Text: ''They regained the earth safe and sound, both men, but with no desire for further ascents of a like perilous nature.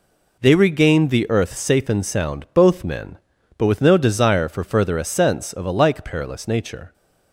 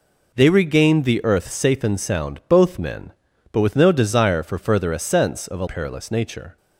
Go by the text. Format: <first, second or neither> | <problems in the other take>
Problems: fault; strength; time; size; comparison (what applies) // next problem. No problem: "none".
first | skips "like"; at 5.6 s